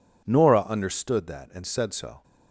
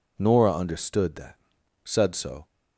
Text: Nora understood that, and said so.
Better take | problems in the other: first | skips "and"; at 1.5 s

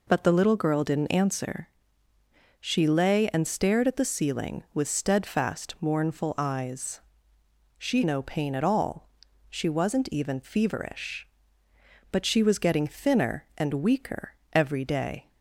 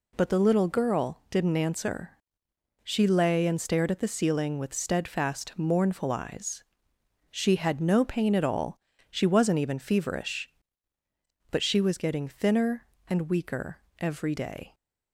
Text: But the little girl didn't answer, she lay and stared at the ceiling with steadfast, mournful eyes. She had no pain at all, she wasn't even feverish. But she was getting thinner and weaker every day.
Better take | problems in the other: second | skips "had"; at 8.0 s // pauses between "weaker" and "every"; slight; at 14.3 s; 0.18 s long; slight in the second

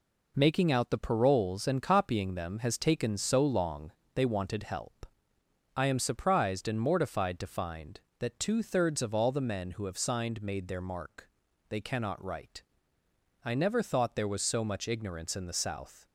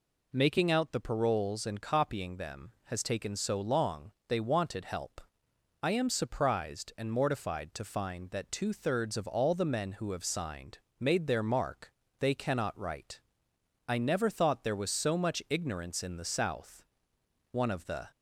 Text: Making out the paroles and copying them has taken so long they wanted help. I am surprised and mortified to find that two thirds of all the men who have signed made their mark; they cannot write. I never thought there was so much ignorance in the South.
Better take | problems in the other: first | pauses between "long" and "they"; slight; at 4.1 s; 0.16 s long; slight in the first // pauses between "signed" and "made"; slight; at 10.7 s; 0.20 s long // goes on to say "One of the"; from 17.5 s on; 0.56 s long

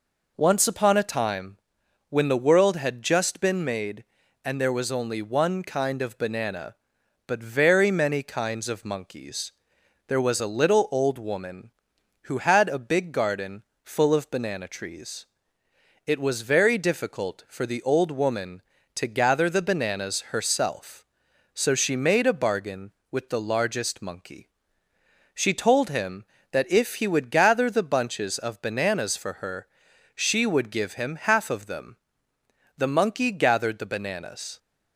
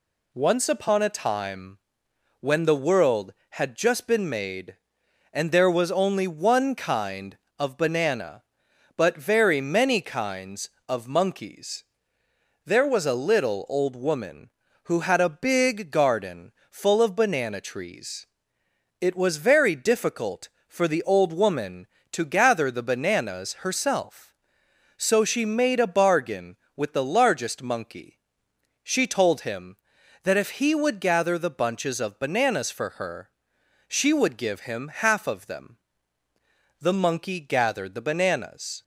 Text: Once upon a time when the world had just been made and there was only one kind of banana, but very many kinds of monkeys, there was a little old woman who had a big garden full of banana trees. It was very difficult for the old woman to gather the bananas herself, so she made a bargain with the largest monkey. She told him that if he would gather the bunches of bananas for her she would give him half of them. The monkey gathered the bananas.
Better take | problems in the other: neither | pauses between "time" and "when"; noticeable; the same in both // pauses between "garden" and "full"; slight; the same in both // pauses between "her" and "she"; noticeable; the same in both

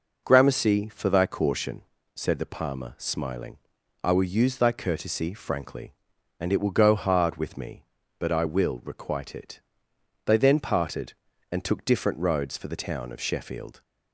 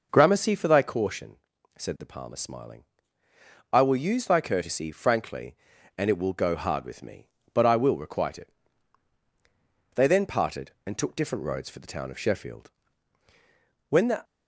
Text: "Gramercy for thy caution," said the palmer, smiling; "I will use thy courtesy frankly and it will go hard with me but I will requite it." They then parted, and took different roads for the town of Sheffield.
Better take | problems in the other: first | goes on to say "When the"; slight; from 13.8 s on; 0.34 s long

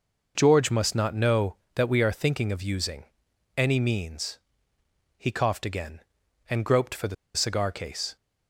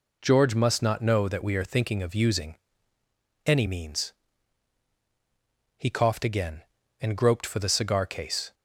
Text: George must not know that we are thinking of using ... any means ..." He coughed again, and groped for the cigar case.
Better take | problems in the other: second | pauses between "the" and "cigar"; slight; at 7.1 s; 0.20 s long

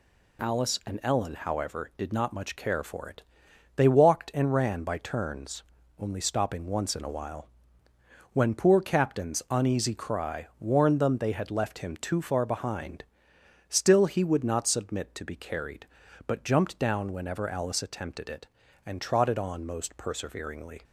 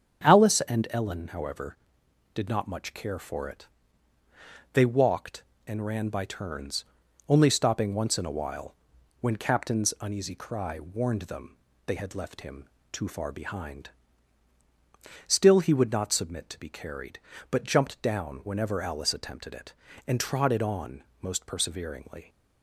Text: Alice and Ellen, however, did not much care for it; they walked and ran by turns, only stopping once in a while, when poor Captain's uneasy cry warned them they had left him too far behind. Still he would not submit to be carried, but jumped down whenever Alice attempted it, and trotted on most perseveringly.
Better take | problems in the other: first | starts louder than the rest; strong; until 1.3 s; 7.5 dB // skips "poor"; at 9.3 s // pauses between "them" and "they"; slight; at 11.5 s; 0.30 s long // pauses between "him" and "too"; slight; at 12.6 s; 0.24 s long // pauses between "on" and "most"; slight; at 21.0 s; 0.20 s long

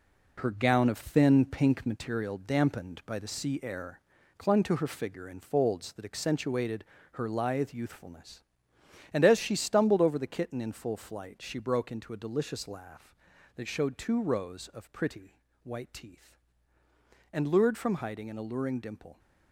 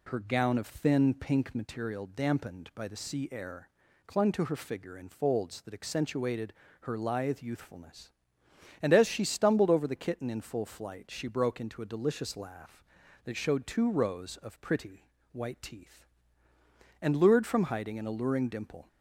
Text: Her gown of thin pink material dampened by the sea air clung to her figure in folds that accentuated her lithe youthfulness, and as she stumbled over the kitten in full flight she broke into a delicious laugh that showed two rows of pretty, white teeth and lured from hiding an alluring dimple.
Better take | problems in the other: second | gets quieter; strong; throughout; 7.5 dB // pauses between "air" and "clung"; at 3.9 s; 0.38 s long; also in the second // pauses between "accentuated" and "her"; slight; at 6.8 s; 0.28 s long; slight in the second

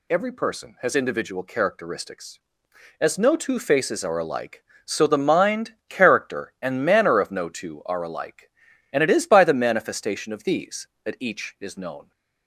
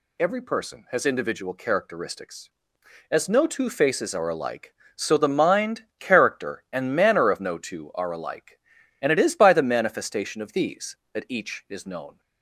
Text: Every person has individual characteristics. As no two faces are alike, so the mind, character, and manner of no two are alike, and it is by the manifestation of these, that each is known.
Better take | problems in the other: neither | none

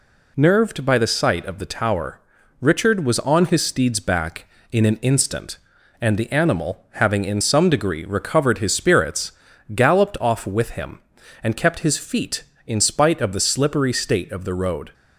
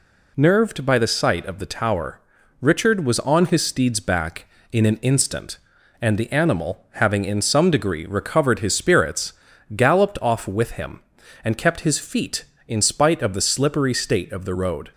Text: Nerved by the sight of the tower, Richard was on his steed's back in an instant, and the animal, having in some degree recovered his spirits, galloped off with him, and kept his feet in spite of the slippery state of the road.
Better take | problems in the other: neither | none

